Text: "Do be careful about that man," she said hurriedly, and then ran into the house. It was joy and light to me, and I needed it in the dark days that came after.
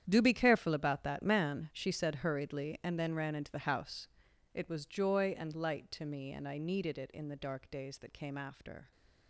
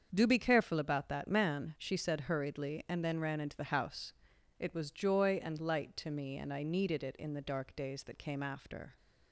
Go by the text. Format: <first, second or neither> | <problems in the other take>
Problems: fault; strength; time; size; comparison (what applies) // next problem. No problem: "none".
second | gets quieter; strong; throughout; 14.5 dB // starts louder than the rest; strong; until 1.0 s; 9.5 dB; also in the second